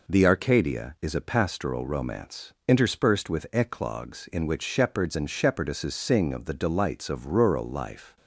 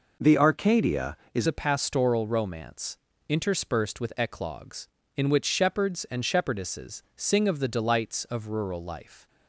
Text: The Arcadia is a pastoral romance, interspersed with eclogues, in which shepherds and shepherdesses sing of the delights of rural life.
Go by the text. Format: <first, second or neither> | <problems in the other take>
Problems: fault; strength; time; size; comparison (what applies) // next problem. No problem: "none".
first | changes voice at "a"; from 1.4 s on; 7.8 s long